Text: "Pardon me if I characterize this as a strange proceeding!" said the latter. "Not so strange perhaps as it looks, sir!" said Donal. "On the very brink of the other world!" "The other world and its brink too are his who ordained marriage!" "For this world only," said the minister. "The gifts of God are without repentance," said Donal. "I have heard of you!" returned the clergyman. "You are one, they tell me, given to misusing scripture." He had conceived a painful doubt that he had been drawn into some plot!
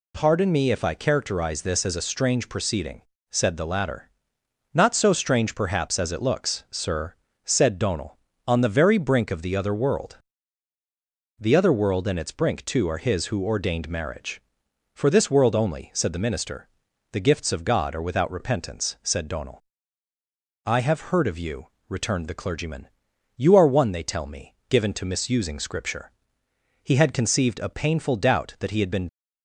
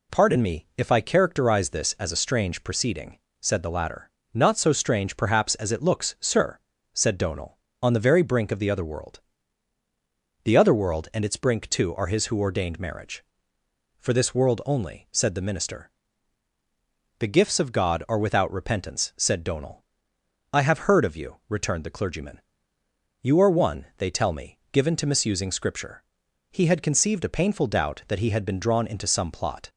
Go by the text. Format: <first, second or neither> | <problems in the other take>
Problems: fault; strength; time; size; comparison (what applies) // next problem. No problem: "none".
second | stops before "drawn into some plot"; at 29.0 s